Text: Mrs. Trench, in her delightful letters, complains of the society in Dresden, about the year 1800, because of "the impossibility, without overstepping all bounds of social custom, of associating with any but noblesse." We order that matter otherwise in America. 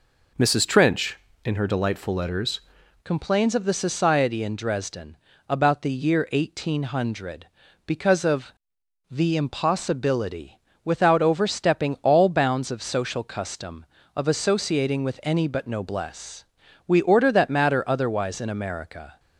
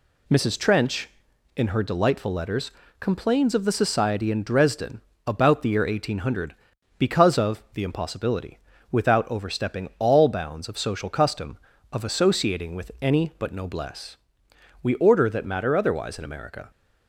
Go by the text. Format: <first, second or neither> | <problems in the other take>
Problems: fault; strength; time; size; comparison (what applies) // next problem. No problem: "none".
second | changes voice at "complains"; from 3.0 s on; 16.1 s long // pauses between "of" and "the"; noticeable; at 8.5 s; 0.60 s long